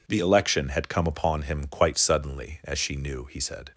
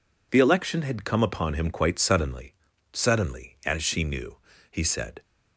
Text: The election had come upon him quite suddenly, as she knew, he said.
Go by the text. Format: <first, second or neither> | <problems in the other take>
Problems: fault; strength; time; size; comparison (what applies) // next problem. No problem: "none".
first | says "suddenly" twice; at 2.9 s